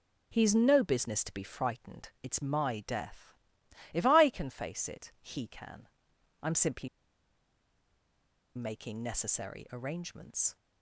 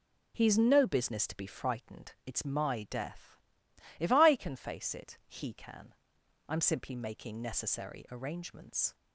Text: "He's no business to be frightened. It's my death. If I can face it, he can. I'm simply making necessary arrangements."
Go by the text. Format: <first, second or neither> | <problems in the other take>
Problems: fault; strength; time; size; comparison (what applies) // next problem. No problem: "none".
second | pauses between "simply" and "making"; strong; at 6.8 s; 1.6 s long